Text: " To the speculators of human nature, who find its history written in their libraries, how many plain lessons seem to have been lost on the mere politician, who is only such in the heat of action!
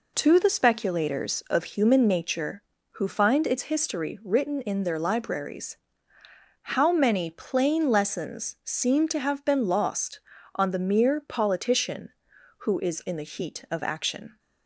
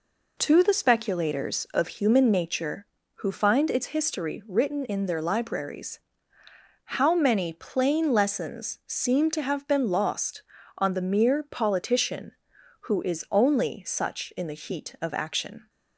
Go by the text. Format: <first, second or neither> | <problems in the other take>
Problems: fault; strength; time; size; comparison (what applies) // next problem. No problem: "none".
second | skips "only such"; at 13.0 s